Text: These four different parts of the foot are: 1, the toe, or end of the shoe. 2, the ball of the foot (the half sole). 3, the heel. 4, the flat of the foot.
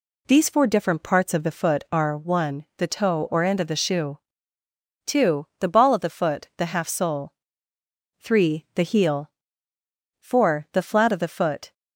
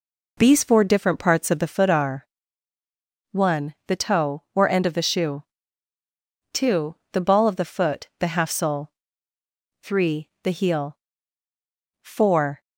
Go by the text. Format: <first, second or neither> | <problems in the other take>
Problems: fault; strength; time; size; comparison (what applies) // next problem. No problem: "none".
first | stops before "the flat of the foot"; at 12.6 s